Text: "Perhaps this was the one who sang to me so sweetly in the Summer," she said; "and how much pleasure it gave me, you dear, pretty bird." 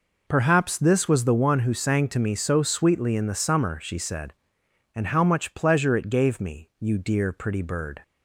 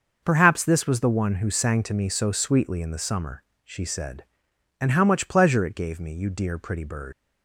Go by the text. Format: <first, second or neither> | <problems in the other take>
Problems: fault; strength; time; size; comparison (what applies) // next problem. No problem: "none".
first | starts louder than the rest; until 1.2 s; 6 dB // leaves "bird" unfinished; at 7.1 s; 100 ms